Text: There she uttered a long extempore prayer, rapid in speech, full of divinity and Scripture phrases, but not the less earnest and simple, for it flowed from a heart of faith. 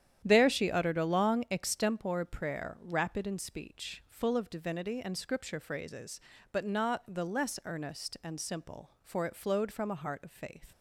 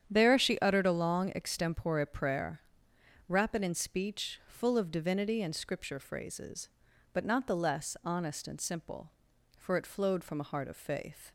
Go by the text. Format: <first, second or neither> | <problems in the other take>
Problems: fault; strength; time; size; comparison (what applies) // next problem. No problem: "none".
first | starts louder than the rest; strong; until 1.1 s; 9 dB; strong in the first // says "honest" for "earnest"; at 8.0 s